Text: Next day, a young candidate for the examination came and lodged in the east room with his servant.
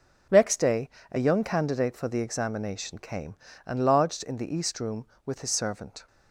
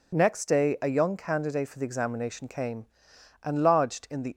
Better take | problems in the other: first | stops before "east room with his servant"; at 4.3 s

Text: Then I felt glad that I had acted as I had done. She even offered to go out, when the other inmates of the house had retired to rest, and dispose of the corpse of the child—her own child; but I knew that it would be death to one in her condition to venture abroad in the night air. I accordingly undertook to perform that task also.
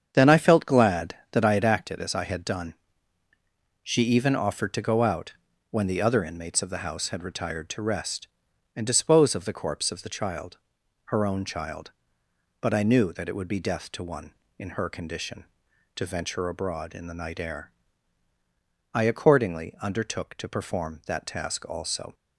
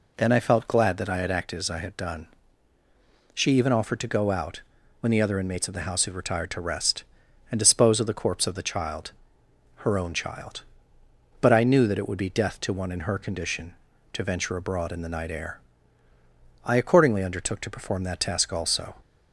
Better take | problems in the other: second | starts louder than the rest; strong; until 1.8 s; 8 dB

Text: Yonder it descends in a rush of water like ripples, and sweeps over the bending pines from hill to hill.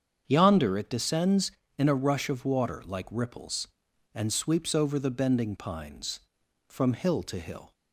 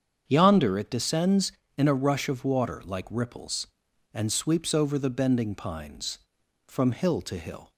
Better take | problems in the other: neither | starts louder than the rest; strong; the same in both

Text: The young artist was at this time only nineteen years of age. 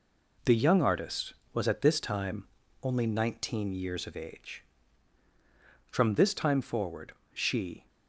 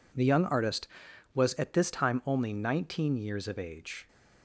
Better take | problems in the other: second | pauses between "time" and "only"; slight; at 2.4 s; 0.36 s long // goes on to say "From this time forward she"; strong; from 5.8 s on; 1.9 s long

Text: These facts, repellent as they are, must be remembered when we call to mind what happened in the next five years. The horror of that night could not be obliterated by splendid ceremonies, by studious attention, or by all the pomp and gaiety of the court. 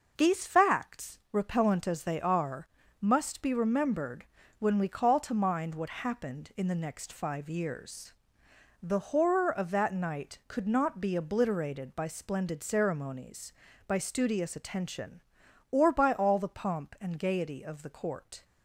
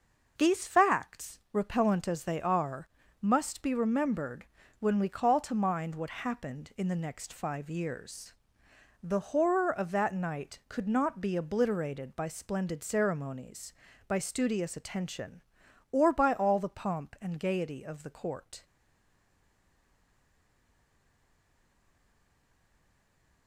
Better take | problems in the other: first | pauses between "remembered" and "when"; slight; at 4.4 s; 0.34 s long; slight in the first // stays silent after the last word; strong; from 18.6 s on; 4.8 s long

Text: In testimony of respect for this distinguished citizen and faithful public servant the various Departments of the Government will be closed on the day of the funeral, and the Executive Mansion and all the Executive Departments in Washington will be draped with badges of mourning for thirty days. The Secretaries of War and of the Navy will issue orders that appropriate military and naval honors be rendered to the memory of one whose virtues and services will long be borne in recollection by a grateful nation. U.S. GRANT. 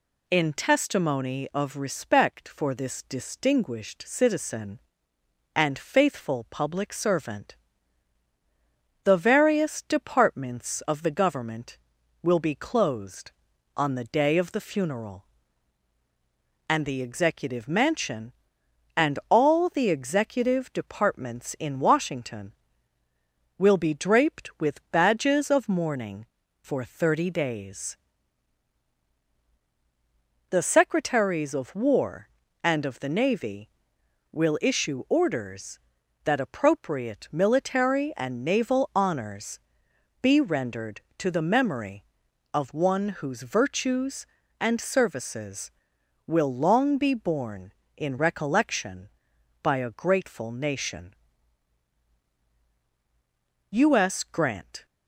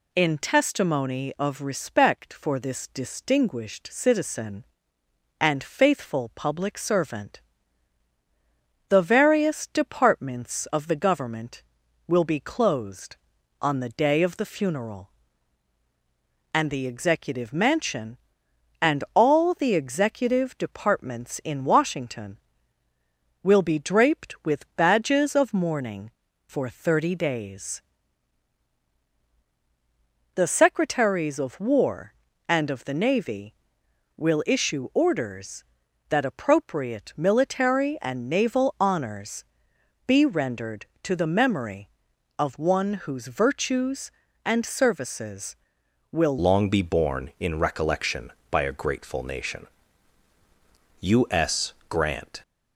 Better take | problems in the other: first | pauses between "servant" and "the"; strong; at 7.3 s; 1.5 s long; strong in the first // pauses between "honors" and "be"; noticeable; at 39.4 s; 0.64 s long; noticeable in the first // changes voice at "long"; from 46.3 s on; 6.1 s long

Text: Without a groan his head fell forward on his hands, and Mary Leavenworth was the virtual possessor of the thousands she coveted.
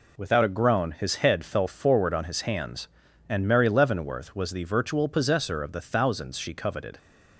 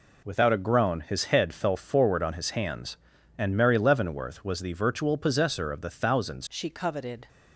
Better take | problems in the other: first | changes voice at "she"; from 6.4 s on; 0.8 s long

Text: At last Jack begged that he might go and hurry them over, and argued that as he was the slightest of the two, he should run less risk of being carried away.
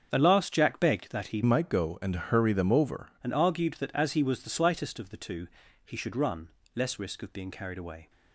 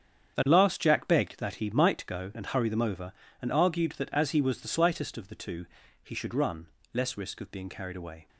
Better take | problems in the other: second | starts louder than the rest; until 1.1 s; 7 dB; strong in the second // changes voice from "might" to "over"; from 1.4 to 3.1 s; 1.7 s long // pauses between "run" and "less"; slight; at 6.4 s; 0.26 s long; slight in the second

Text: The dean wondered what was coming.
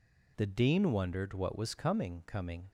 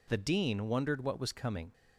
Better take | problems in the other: second | says "coming" twice; at 2.2 s

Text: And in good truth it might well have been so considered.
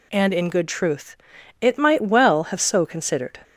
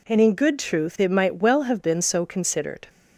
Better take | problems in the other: second | pauses between "truth" and "it"; at 1.1 s; 0.42 s long // skips "been"; at 2.5 s

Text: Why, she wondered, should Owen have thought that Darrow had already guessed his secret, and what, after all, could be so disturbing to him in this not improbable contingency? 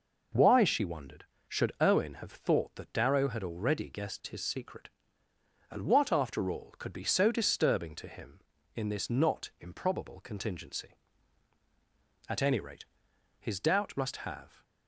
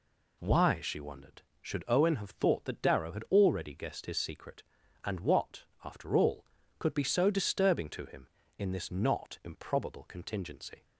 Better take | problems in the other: second | goes on to say "At any rate his doubt must have"; strong; from 12.2 s on; 2.3 s long

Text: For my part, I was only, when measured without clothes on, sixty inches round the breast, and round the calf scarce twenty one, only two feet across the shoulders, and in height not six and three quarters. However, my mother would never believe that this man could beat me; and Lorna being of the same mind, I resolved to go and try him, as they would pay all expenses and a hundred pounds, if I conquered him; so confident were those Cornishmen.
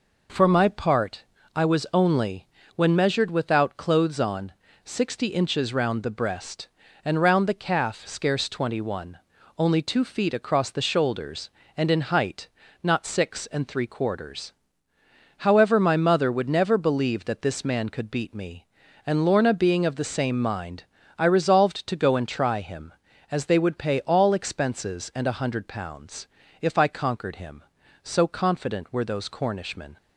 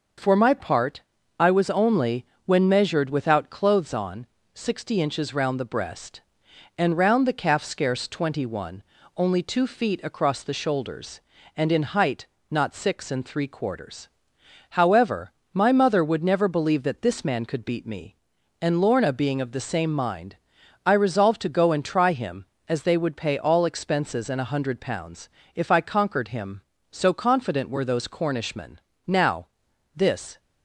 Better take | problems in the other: first | starts louder than the rest; until 1.5 s; 6 dB // pauses between "height" and "not"; slight; at 12.2 s; 0.26 s long; slight in the first // goes on to say "Now this"; from 29.0 s on; 1.3 s long

